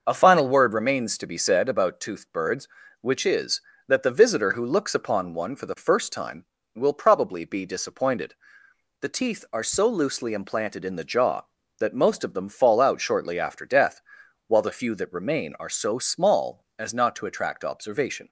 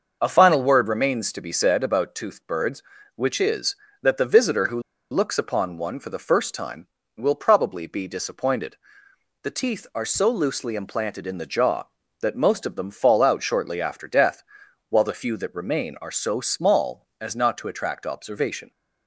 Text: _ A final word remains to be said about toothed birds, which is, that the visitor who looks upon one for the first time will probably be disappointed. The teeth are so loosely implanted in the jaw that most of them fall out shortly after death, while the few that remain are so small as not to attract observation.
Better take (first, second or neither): first